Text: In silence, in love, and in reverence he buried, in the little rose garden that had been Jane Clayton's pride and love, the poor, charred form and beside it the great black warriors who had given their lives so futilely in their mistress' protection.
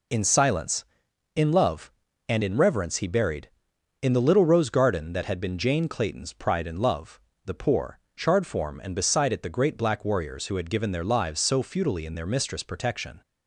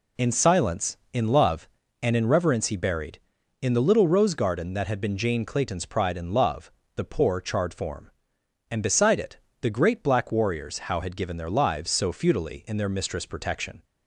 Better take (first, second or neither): first